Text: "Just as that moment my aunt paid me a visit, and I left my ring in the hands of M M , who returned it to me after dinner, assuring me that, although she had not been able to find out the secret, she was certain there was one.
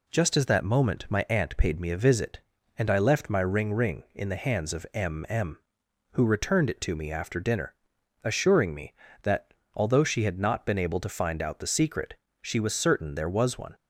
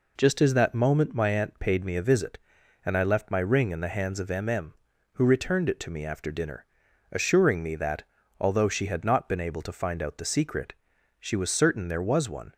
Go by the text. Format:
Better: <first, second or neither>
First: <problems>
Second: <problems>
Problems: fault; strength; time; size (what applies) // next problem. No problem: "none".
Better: second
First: says "ring" twice; at 3.7 s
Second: none